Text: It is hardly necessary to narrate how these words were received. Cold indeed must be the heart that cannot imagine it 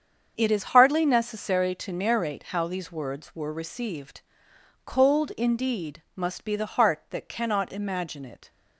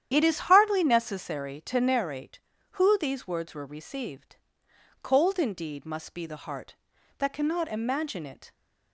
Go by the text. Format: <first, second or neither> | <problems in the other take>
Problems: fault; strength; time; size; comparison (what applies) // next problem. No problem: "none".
first | starts louder than the rest; strong; until 1.1 s; 10 dB; strong in the first // says "who" for "how"; at 2.7 s